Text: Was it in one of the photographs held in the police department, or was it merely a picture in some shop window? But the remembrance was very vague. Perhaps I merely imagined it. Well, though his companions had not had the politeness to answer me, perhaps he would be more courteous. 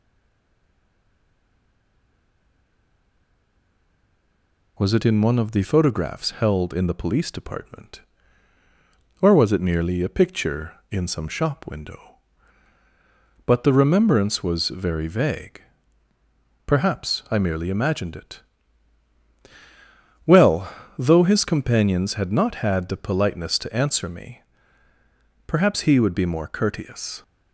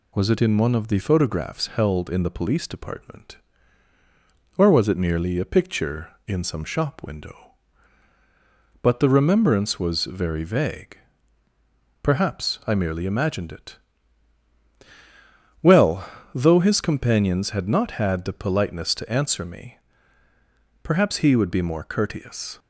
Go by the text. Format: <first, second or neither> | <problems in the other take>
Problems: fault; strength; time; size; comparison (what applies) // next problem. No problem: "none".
second | stays silent before the first word; strong; until 4.7 s; 4.7 s long